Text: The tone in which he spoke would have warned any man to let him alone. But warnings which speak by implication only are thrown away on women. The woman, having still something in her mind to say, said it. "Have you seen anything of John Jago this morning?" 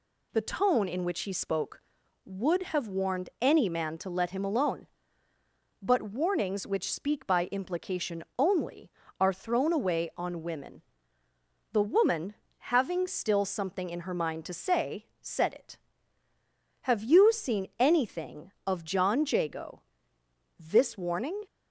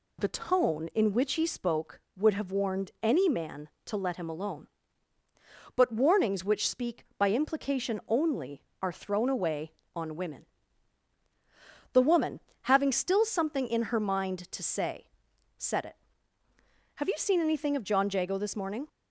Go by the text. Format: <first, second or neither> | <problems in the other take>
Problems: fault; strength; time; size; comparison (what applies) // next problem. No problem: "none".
second | pauses between "implication" and "only"; slight; at 8.2 s; 0.16 s long // pauses between "Jago" and "this"; noticeable; at 19.8 s; 0.78 s long // says "warning" for "morning"; at 20.9 s